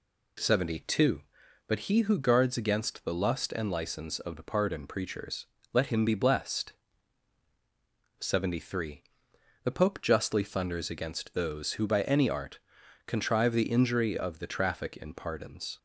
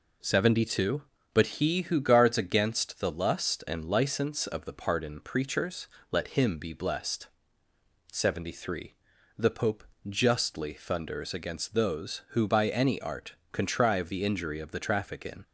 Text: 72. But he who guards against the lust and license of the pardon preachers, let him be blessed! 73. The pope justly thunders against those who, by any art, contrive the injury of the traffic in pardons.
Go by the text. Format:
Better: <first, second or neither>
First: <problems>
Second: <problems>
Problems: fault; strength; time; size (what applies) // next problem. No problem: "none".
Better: first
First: none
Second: pauses between "pope" and "justly"; slight; at 9.8 s; 0.24 s long // stops before "pardons"; at 15.4 s